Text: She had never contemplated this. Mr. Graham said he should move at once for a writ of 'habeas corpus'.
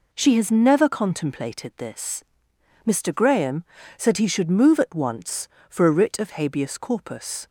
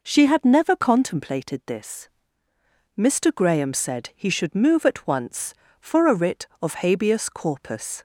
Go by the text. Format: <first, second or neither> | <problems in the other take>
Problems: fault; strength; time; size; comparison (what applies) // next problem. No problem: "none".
second | says "has" for "had"; at 0.3 s // pauses between "Graham" and "said"; slight; at 3.6 s; 0.32 s long